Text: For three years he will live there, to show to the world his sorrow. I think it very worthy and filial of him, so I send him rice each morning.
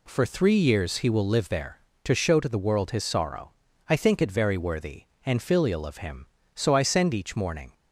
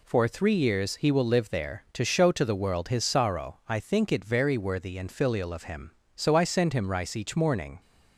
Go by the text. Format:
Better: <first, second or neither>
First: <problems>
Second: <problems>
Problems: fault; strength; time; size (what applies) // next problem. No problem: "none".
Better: second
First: skips "him rice"; at 7.1 s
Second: none